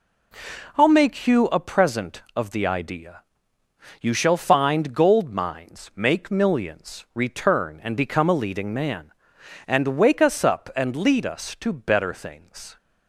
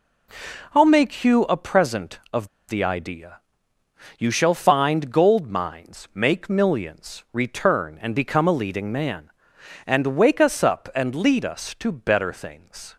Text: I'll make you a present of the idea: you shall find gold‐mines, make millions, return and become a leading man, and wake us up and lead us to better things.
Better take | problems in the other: first | pauses between "of" and "the"; slight; at 2.4 s; 0.21 s long

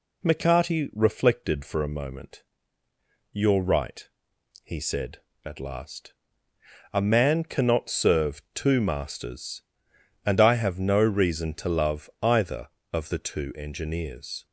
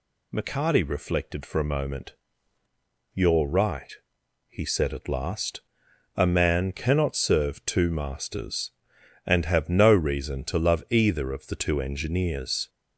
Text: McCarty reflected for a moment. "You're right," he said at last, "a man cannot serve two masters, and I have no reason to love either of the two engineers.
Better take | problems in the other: first | skips "I"; at 9.4 s

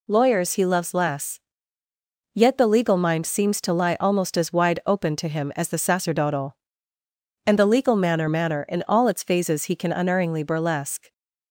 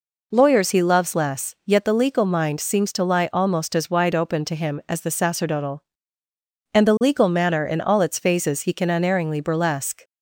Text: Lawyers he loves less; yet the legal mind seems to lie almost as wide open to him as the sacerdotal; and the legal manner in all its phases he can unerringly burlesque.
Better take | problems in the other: second | says "manner" twice; at 8.2 s

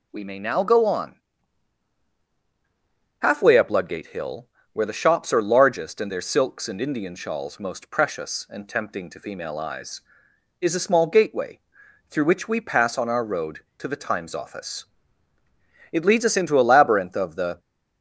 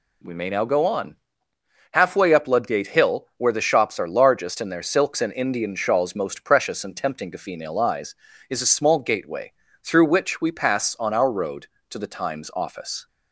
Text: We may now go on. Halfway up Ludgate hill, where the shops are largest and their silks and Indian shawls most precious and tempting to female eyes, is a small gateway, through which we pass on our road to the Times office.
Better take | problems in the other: second | goes on to say "It leads us into a labyrinth of the"; strong; from 15.9 s on; 1.6 s long

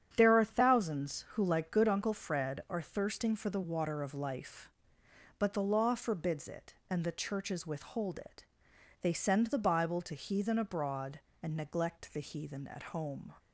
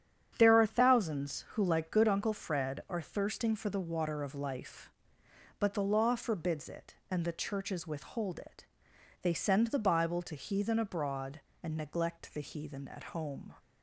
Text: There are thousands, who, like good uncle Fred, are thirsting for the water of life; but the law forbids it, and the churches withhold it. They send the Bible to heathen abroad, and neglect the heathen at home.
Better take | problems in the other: neither | starts louder than the rest; strong; the same in both

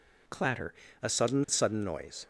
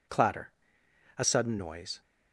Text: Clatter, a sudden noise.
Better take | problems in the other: second | says "sudden" twice; at 1.4 s

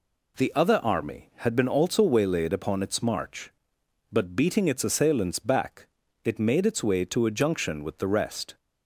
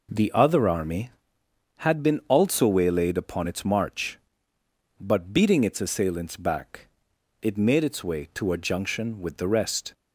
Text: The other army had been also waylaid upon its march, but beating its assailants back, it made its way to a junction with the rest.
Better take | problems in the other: neither | none

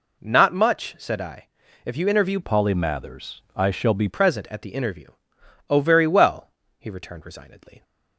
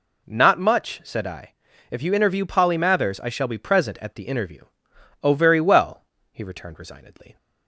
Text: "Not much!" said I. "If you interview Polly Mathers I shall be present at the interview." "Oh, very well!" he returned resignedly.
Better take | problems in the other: second | changes voice from "Polly" to "be"; from 2.4 to 4.0 s; 1.6 s long

